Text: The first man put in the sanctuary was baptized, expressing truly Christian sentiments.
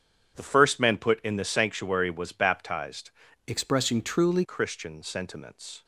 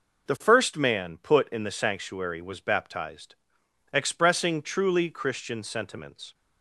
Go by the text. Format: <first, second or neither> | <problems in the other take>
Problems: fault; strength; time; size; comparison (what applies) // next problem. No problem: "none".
second | starts louder than the rest; strong; until 1.3 s; 7.5 dB // changes voice from "expressing" to "truly"; from 3.4 to 4.4 s; 1.0 s long